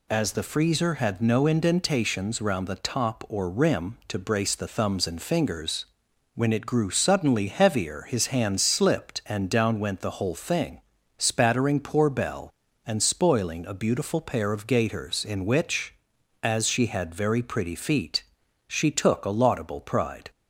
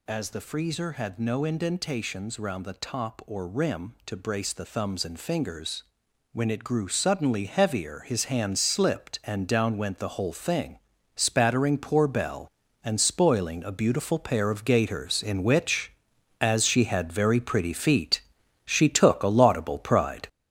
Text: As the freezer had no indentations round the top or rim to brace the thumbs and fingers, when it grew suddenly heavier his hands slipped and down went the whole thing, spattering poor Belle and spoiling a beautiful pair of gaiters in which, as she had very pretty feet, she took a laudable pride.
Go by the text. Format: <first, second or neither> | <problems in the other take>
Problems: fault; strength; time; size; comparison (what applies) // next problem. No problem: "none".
first | gets louder; throughout; 7 dB